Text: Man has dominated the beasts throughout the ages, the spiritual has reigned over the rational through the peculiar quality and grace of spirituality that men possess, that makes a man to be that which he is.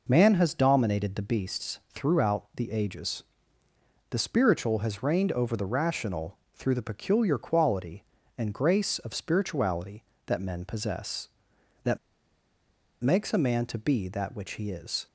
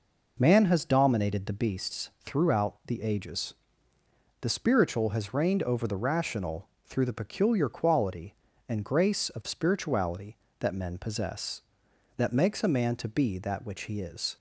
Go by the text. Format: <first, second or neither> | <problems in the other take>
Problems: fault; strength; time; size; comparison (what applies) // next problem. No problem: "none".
second | pauses between "rational" and "through"; slight; at 6.3 s; 0.18 s long; slight in the second // pauses between "that" and "makes"; at 11.9 s; 1.0 s long